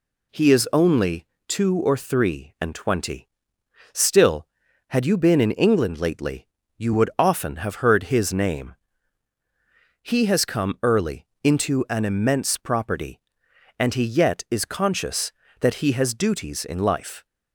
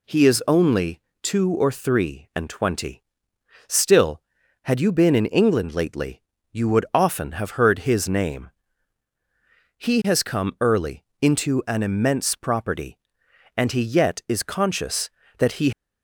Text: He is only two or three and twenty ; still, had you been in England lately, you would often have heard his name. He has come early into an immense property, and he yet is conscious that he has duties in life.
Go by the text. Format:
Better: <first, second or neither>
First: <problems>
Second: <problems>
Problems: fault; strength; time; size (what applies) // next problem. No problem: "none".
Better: first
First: pauses between "only" and "two"; slight; at 1.2 s; 0.22 s long // pauses between "early" and "into"; slight; at 11.2 s; 0.16 s long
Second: pauses between "only" and "two"; slight; at 1.0 s; 0.22 s long // pauses between "early" and "into"; slight; at 11.0 s; 0.16 s long // stops before "has duties in life"; at 15.7 s